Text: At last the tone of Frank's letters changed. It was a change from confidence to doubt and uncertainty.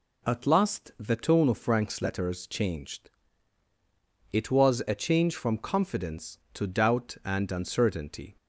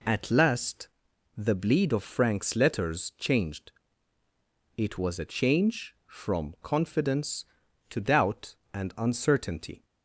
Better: first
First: none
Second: pauses between "last" and "the"; noticeable; at 0.8 s; 0.48 s long // says "bleed" for "tone"; at 1.5 s

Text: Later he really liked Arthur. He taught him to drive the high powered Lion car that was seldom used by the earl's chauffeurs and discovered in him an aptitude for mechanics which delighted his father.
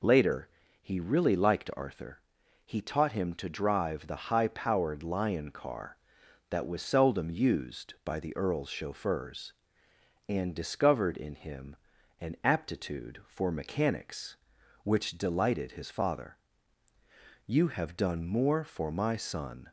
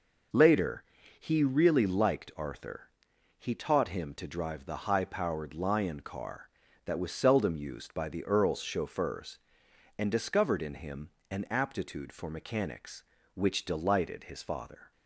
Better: second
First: pauses between "Later" and "he"; slight; at 0.4 s; 0.34 s long // pauses between "him" and "an"; noticeable; at 11.7 s; 0.46 s long // goes on to say "You have done more for my son"; strong; from 17.4 s on; 2.2 s long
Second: pauses between "Later" and "he"; slight; at 0.8 s; 0.34 s long // pauses between "him" and "an"; slight; at 11.1 s; 0.18 s long

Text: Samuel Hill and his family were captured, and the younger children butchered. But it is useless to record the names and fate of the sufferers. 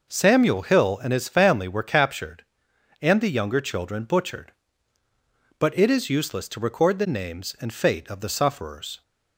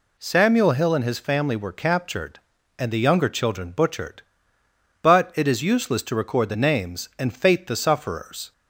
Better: first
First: none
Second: skips "of"; at 7.6 s

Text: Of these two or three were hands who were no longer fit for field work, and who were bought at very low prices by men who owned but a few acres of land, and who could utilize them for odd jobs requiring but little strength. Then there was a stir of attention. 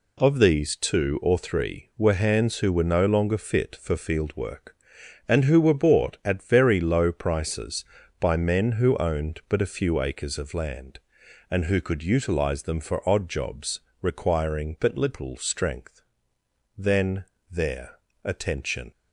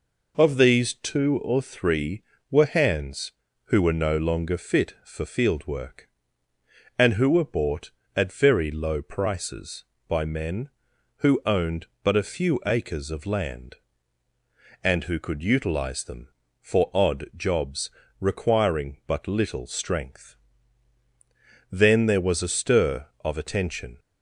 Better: second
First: pauses between "jobs" and "requiring"; slight; at 13.7 s; 0.22 s long // pauses between "Then" and "there"; slight; at 17.2 s; 0.26 s long // skips "was a stir of"; at 18.1 s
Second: pauses between "jobs" and "requiring"; slight; at 17.8 s; 0.30 s long

